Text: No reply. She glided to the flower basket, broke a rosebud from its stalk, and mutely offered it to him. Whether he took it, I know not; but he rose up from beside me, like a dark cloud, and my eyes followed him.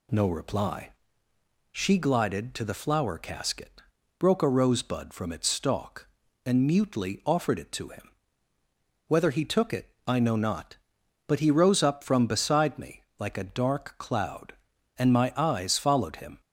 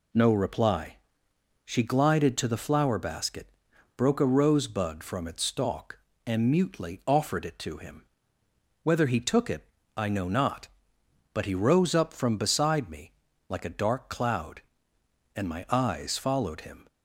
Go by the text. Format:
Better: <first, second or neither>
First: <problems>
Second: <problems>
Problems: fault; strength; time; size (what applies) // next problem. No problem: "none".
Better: second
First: says "casket" for "basket"; at 3.1 s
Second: none